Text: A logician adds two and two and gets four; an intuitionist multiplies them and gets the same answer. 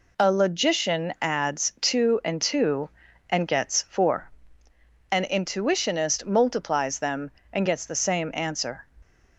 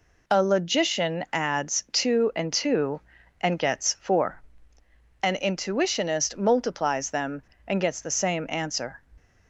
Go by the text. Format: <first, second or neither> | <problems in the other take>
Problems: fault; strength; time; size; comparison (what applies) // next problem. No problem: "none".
neither | none